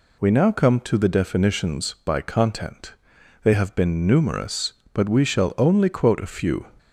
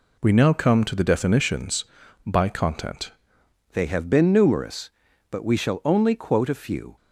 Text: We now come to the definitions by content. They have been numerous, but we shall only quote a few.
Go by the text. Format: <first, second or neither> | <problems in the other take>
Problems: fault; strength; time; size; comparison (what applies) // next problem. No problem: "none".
first | changes voice at "They"; from 3.7 s on; 3.2 s long